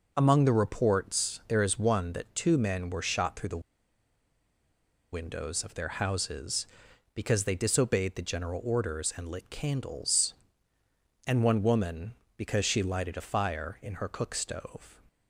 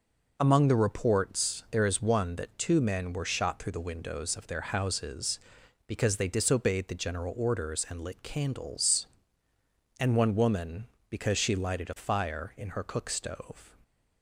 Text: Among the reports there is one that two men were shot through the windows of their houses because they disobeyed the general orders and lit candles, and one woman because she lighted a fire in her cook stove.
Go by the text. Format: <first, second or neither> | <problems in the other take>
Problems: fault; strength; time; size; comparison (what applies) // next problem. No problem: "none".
second | pauses between "the" and "windows"; strong; at 3.6 s; 1.5 s long